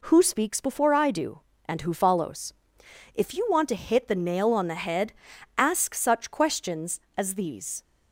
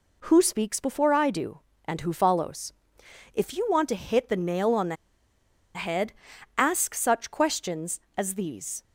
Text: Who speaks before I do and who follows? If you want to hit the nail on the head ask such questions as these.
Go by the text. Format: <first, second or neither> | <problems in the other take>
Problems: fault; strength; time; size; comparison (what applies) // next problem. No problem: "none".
first | pauses between "the" and "head"; noticeable; at 4.9 s; 0.79 s long // pauses between "head" and "ask"; at 6.1 s; 0.44 s long; also in the first